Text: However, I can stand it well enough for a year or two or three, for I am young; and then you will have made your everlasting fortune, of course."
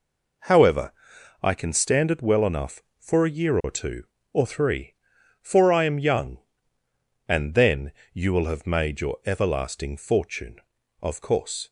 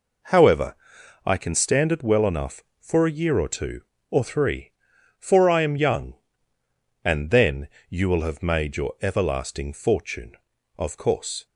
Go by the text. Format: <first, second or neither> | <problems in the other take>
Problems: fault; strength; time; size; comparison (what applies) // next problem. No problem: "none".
neither | pauses between "then" and "you"; slight; the same in both